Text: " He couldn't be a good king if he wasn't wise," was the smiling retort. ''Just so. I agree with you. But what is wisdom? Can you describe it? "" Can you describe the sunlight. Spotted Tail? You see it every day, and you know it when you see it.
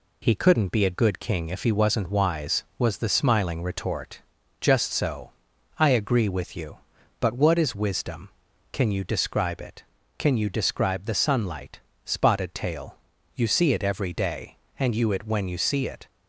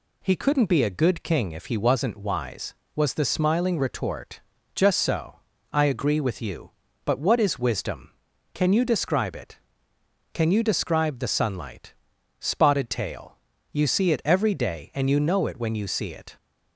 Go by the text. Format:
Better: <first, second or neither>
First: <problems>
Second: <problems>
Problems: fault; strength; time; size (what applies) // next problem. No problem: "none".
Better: second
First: skips "know"; at 15.0 s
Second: none